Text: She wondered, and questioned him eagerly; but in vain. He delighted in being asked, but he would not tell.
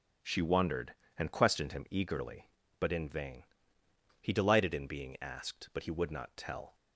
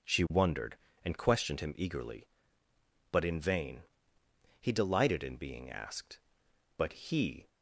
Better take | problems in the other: first | stops before "would not tell"; at 7.4 s

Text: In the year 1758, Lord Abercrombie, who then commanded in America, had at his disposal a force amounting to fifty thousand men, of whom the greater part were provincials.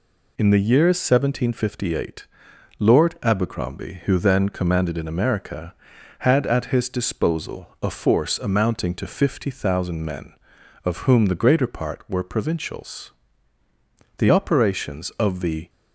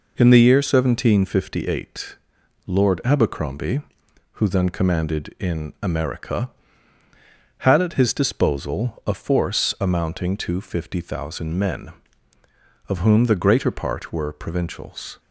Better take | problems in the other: second | goes on to say "The operations of the"; from 14.1 s on; 1.5 s long

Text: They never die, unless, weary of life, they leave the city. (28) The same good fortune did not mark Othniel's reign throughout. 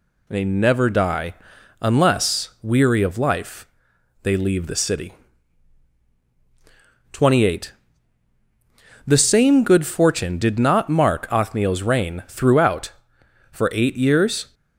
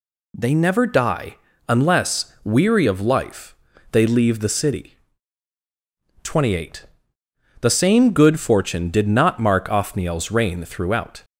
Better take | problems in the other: second | goes on to say "For eight years"; noticeable; from 13.5 s on; 1.0 s long

